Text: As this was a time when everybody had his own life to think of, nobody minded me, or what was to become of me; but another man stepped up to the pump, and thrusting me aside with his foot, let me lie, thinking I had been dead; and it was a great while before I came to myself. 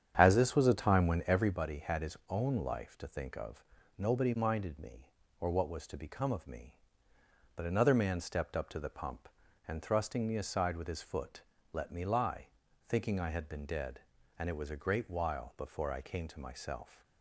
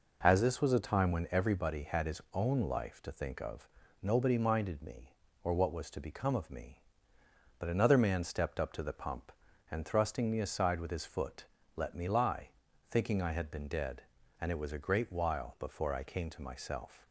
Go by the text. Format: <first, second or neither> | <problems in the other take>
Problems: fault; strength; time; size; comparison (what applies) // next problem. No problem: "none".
second | starts louder than the rest; strong; until 1.6 s; 8.5 dB